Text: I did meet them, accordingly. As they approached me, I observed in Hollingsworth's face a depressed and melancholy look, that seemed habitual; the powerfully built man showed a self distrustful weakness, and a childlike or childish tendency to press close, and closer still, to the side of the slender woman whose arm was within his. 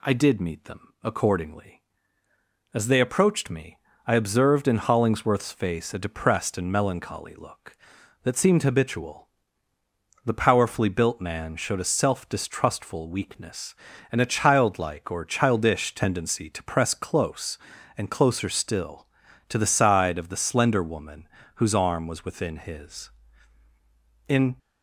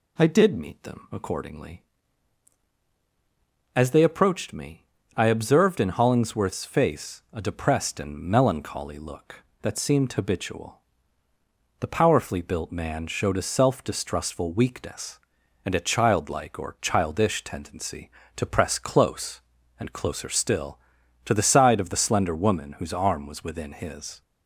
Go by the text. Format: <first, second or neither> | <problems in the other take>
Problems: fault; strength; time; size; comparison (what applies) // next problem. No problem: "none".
second | pauses between "woman" and "whose"; slight; at 21.2 s; 0.28 s long // goes on to say "In"; slight; from 24.2 s on; 0.28 s long